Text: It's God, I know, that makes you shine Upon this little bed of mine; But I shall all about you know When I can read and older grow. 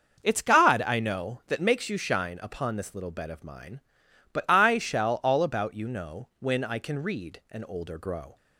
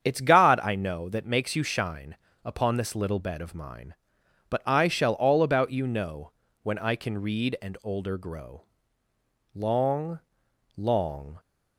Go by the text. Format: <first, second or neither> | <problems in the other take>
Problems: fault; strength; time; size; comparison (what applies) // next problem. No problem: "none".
first | starts louder than the rest; strong; until 1.0 s; 8 dB; also in the first // pauses between "shine" and "Upon"; slight; at 2.1 s; 0.28 s long // pauses between "know" and "When"; slight; at 6.3 s; 0.30 s long // goes on to say "Long long"; strong; from 9.5 s on; 1.8 s long